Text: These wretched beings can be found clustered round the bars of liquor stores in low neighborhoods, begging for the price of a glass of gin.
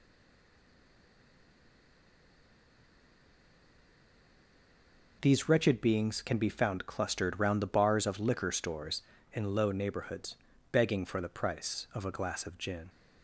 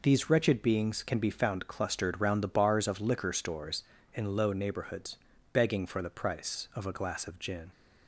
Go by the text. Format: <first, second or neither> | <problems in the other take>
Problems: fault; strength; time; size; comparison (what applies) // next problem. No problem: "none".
second | stays silent before the first word; strong; until 5.2 s; 5.2 s long